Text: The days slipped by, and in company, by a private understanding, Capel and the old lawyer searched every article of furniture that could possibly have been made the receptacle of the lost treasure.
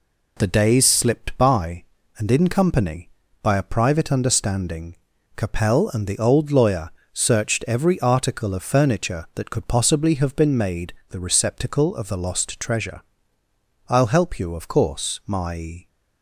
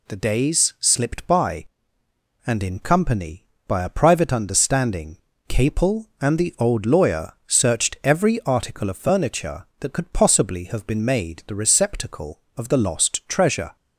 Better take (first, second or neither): second